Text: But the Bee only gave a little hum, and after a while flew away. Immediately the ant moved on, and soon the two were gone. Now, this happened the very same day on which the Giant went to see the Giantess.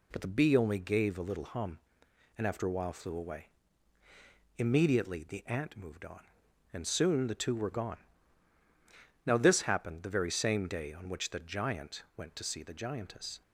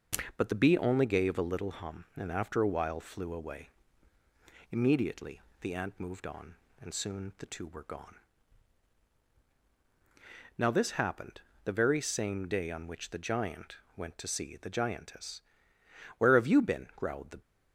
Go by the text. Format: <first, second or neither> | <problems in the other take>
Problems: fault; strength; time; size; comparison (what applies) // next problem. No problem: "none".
first | pauses between "Immediately" and "the"; slight; at 5.3 s; 0.22 s long // pauses between "happened" and "the"; slight; at 11.3 s; 0.24 s long // pauses between "Giant" and "went"; slight; at 13.7 s; 0.20 s long // goes on to say "Where have you been growled the"; noticeable; from 16.1 s on; 1.2 s long